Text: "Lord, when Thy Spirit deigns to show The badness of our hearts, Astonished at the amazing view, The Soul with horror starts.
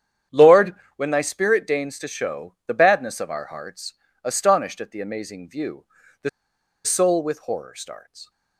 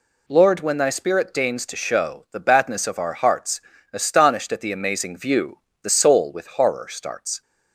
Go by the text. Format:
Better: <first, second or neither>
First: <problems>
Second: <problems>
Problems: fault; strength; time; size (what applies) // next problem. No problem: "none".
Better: second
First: starts louder than the rest; strong; until 1.5 s; 9 dB // pauses between "The" and "Soul"; noticeable; at 6.2 s; 0.55 s long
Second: none